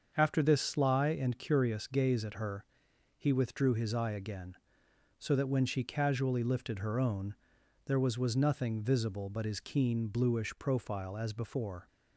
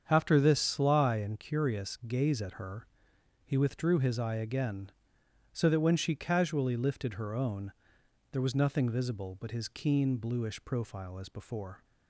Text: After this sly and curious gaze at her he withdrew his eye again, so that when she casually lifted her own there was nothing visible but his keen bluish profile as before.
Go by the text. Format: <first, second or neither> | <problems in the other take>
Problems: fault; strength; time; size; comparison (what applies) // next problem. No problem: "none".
second | starts louder than the rest; until 1.1 s; 7 dB; strong in the second // pauses between "her" and "he"; noticeable; at 2.6 s; 0.52 s long; noticeable in the second // pauses between "own" and "there"; noticeable; at 7.3 s; 0.50 s long; noticeable in the second // says "was" twice; at 8.1 s